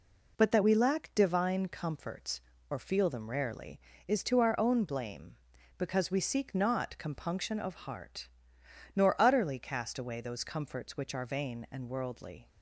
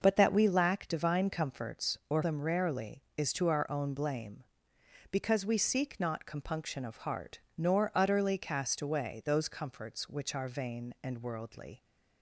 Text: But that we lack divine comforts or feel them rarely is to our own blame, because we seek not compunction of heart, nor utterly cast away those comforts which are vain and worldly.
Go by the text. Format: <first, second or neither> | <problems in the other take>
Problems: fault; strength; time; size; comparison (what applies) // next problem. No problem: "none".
first | skips "feel"; at 2.2 s